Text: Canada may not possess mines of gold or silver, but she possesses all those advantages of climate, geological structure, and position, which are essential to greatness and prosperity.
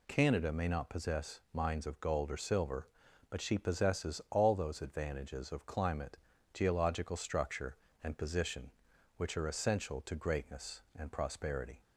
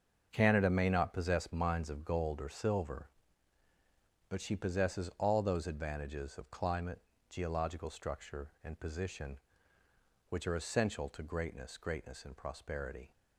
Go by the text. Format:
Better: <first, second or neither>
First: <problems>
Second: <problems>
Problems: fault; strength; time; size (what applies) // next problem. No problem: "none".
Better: first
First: none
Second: starts louder than the rest; until 1.3 s; 6.5 dB // says "greatness" twice; at 11.7 s